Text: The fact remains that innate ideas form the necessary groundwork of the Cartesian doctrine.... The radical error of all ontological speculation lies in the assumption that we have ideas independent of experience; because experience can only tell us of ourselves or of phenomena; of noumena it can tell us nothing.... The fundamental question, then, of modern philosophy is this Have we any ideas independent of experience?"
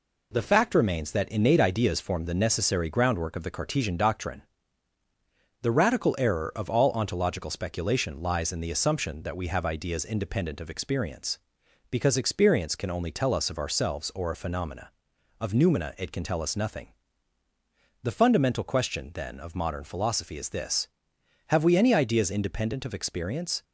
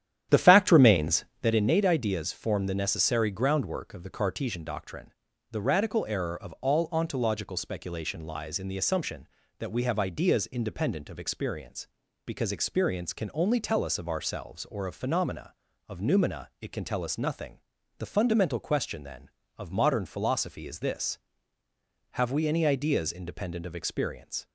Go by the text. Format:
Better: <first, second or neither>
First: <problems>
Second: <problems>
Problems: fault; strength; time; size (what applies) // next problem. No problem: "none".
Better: first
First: none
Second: starts louder than the rest; strong; until 1.6 s; 10.5 dB